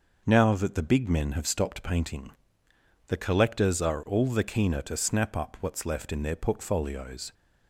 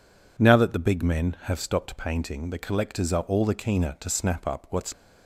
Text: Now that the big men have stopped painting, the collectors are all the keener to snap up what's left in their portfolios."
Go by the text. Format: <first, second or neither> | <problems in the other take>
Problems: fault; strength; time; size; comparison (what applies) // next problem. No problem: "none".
first | stops before "left in their portfolios"; at 4.9 s